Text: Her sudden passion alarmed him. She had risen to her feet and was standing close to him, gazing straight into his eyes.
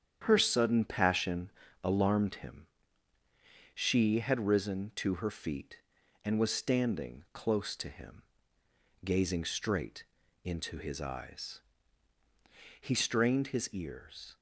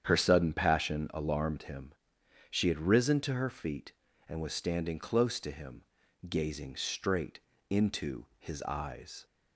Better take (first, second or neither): second